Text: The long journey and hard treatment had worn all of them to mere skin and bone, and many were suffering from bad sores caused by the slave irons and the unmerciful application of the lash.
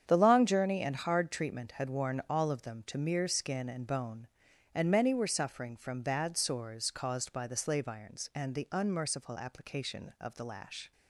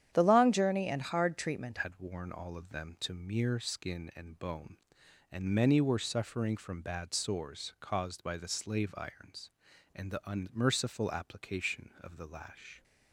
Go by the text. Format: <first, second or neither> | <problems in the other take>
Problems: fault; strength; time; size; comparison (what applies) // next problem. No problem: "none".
first | starts louder than the rest; strong; until 1.1 s; 10 dB; strong in the first // changes voice at "had"; from 1.7 s on; 11.1 s long